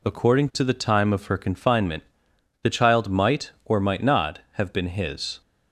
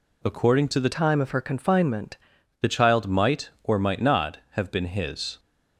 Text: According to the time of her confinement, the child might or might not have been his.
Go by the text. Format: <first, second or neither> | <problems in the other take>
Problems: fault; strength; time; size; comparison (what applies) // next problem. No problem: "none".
first | changes voice from "time" to "confinement"; from 0.9 to 2.1 s; 1.2 s long